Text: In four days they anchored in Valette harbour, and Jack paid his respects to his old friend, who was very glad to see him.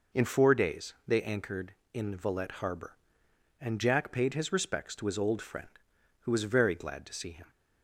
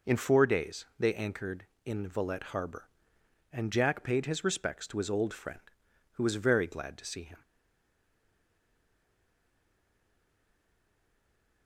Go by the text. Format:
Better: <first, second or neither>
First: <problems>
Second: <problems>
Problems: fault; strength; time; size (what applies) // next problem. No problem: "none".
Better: first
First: none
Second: stays silent after the last word; strong; from 7.4 s on; 4.2 s long